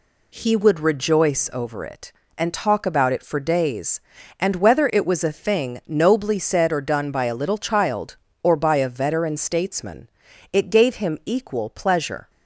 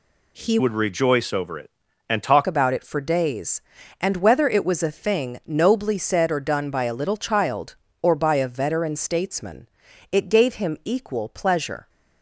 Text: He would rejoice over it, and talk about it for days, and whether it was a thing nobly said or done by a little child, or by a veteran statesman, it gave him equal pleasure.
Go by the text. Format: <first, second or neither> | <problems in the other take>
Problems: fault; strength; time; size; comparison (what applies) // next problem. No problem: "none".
first | changes voice from "would" to "talk"; from 0.5 to 2.4 s; 1.9 s long